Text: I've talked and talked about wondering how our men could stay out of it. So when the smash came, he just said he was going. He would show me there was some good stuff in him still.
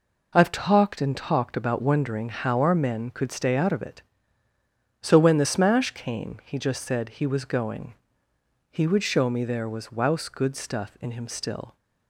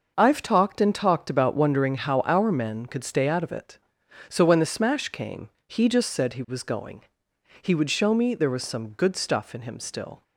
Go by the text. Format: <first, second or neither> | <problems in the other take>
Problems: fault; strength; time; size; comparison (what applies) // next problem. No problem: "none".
second | says "wouse" for "some"; at 9.9 s